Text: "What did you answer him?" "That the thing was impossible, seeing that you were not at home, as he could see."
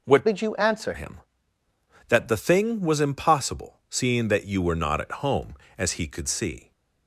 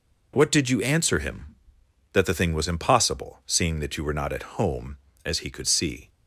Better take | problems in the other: second | changes voice from "did" to "answer"; from 0.2 to 0.9 s; 0.7 s long

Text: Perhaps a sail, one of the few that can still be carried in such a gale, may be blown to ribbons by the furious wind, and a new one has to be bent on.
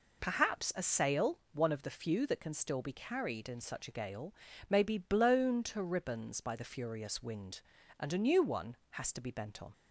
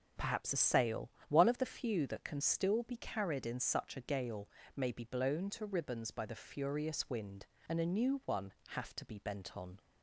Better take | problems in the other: first | says "have" for "has"; at 8.6 s

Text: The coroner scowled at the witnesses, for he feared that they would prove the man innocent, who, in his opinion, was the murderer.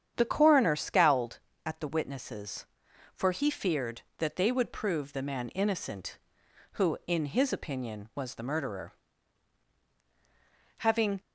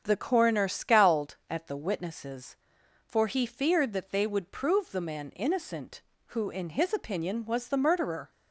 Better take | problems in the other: second | starts louder than the rest; strong; until 1.1 s; 9 dB; strong in the second // goes on to say "Having"; slight; from 10.7 s on; 0.42 s long

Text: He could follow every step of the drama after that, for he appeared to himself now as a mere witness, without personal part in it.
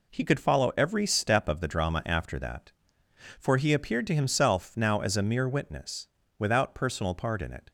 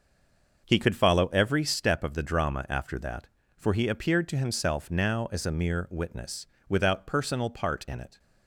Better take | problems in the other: first | stays silent before the first word; slight; until 0.6 s; 0.6 s long // starts louder than the rest; noticeable; until 1.6 s; 6 dB

